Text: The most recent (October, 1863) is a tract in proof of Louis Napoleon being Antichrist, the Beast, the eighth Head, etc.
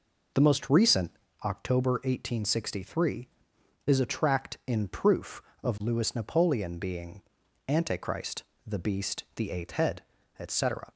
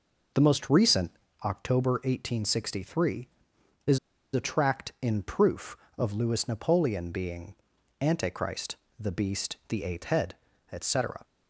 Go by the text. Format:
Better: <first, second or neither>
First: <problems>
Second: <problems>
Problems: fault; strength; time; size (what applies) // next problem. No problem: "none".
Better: first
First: pauses between "being" and "Antichrist"; noticeable; at 7.2 s; 0.48 s long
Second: pauses between "is" and "a"; slight; at 3.9 s; 0.35 s long // pauses between "being" and "Antichrist"; noticeable; at 7.5 s; 0.48 s long